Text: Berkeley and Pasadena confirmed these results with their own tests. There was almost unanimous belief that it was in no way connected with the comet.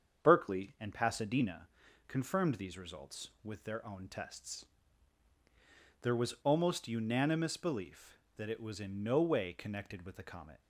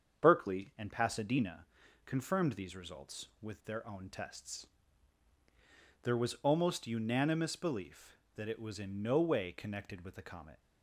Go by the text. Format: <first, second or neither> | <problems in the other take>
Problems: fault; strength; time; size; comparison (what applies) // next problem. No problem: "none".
neither | starts louder than the rest; strong; the same in both // pauses between "Pasadena" and "confirmed"; the same in both